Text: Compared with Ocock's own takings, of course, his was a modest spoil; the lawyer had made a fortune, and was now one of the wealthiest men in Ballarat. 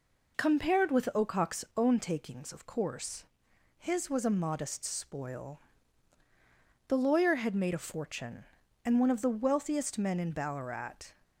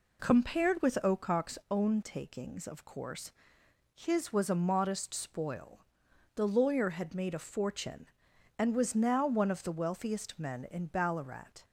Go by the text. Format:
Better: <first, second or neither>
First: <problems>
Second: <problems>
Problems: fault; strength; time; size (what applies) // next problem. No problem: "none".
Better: second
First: skips "was now"; at 8.9 s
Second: none